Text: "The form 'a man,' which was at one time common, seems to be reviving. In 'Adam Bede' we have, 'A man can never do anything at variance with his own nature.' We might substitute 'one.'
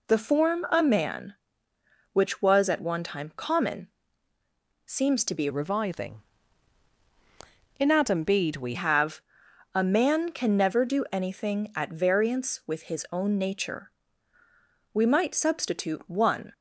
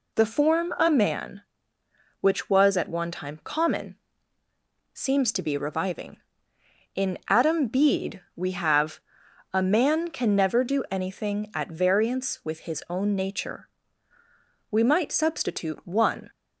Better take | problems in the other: second | changes voice from "reviving" to "we"; from 5.5 to 8.7 s; 3.2 s long

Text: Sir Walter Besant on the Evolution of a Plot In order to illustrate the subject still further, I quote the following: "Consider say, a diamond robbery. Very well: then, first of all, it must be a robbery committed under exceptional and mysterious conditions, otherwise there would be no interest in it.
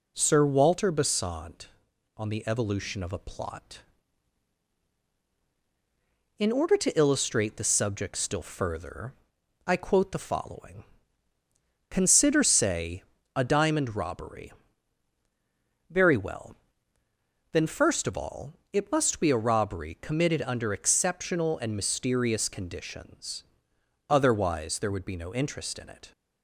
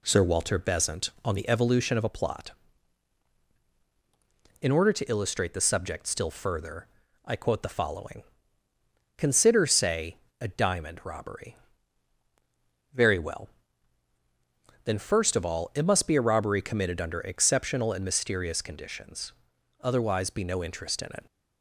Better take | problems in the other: first | skips "there would"; at 20.2 s

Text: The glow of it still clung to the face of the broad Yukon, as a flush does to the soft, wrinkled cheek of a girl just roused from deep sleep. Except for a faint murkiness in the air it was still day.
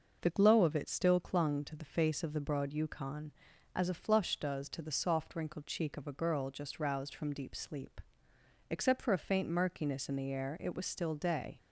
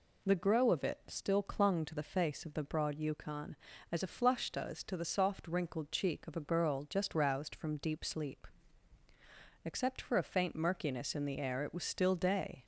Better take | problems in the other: first | says "grow" for "glow"; at 0.3 s

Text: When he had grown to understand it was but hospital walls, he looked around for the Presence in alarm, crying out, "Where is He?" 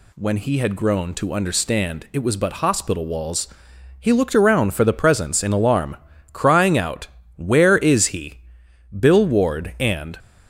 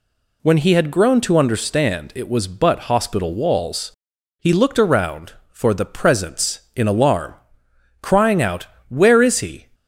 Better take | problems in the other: second | goes on to say "Bill Ward and"; noticeable; from 8.9 s on; 1.2 s long

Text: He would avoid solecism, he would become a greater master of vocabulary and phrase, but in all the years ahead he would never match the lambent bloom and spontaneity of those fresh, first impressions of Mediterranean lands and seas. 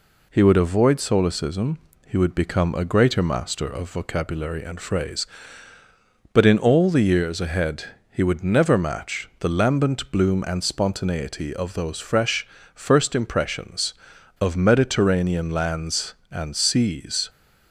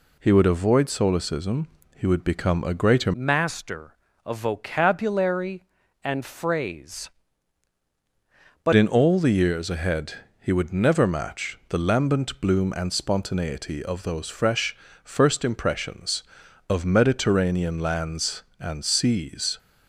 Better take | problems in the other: first | changes voice from "master" to "but"; from 3.1 to 8.7 s; 5.6 s long // pauses between "ahead" and "he"; slight; at 10.1 s; 0.26 s long; slight in the first

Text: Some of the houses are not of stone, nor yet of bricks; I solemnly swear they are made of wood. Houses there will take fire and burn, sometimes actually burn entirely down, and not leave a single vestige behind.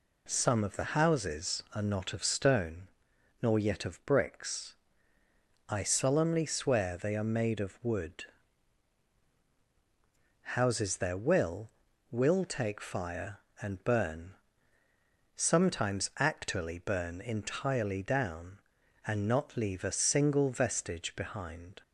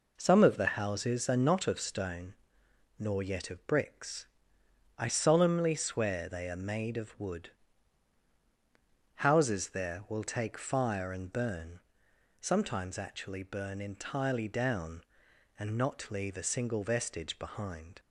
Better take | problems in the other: second | says "will" twice; at 12.1 s

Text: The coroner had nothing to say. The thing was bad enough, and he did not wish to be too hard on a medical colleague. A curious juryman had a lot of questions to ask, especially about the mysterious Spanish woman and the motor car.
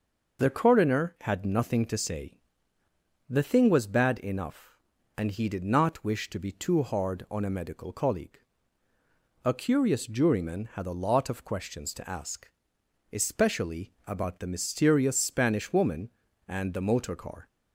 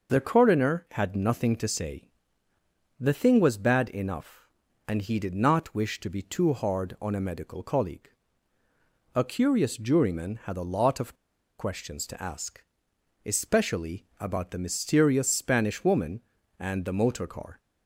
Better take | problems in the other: first | pauses between "of" and "questions"; at 11.1 s; 0.43 s long

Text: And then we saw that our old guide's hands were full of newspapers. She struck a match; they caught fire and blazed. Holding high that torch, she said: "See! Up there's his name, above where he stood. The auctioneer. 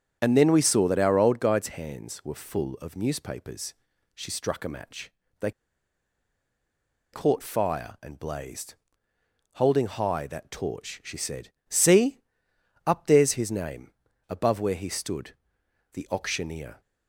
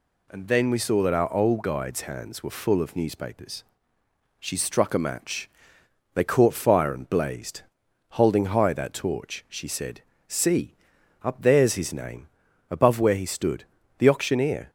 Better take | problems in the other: second | starts louder than the rest; strong; until 1.2 s; 8 dB // pauses between "they" and "caught"; strong; at 5.5 s; 1.6 s long

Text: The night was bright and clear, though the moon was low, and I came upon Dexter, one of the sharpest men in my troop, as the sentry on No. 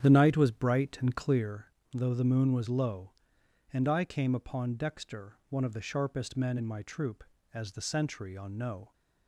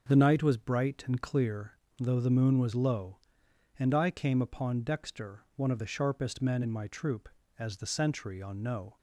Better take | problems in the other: second | starts louder than the rest; strong; until 1.6 s; 9 dB

